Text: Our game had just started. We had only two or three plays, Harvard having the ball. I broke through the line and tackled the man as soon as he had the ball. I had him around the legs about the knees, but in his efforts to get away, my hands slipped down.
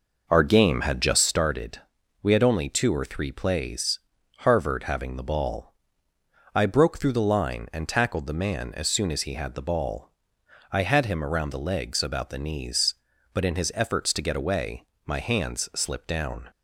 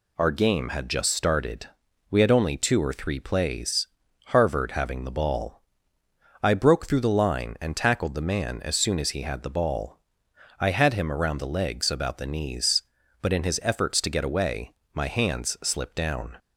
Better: second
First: starts louder than the rest; noticeable; until 1.4 s; 5.5 dB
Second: none

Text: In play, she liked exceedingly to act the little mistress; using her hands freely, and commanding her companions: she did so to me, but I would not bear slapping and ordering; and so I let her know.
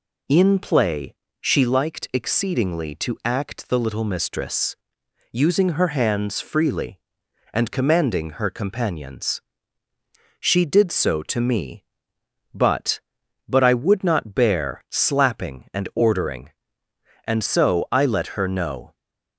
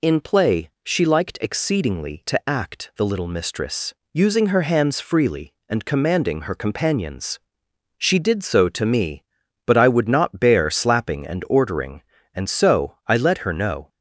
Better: second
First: says "but" twice; at 13.4 s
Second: none

